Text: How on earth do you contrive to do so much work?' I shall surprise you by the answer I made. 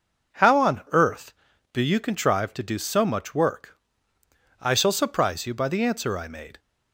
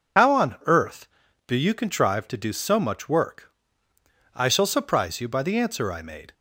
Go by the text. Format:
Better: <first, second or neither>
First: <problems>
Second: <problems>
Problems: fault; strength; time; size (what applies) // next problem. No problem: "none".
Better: first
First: none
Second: loses the start of "How"; at 0.1 s; 90 ms